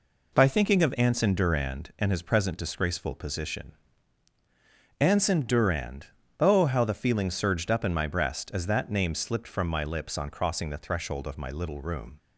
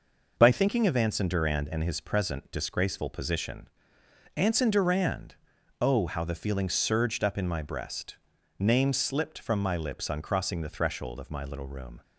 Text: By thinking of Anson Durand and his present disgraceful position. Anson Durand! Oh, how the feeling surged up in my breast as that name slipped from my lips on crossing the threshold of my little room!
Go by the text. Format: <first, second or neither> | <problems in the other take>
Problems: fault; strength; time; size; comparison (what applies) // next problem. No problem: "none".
first | skips "as that"; at 8.3 s